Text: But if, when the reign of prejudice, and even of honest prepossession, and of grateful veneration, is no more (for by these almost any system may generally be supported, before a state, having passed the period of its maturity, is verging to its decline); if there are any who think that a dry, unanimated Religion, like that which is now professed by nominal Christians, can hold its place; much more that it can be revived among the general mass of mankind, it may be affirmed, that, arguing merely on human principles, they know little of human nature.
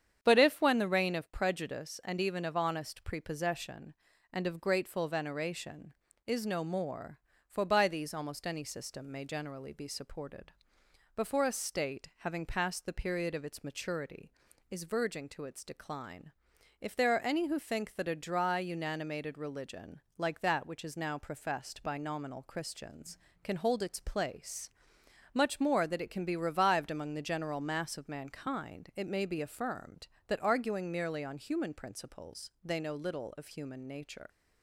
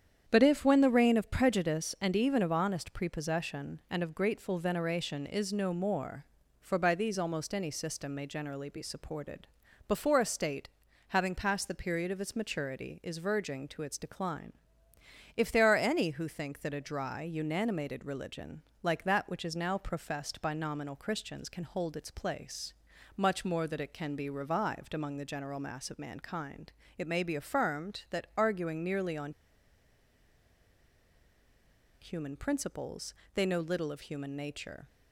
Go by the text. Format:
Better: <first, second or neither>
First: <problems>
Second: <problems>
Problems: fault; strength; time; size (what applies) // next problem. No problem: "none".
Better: first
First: starts louder than the rest; strong; until 1.2 s; 8.5 dB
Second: starts louder than the rest; strong; until 1.2 s; 8.5 dB // pauses between "on" and "human"; strong; at 29.3 s; 2.6 s long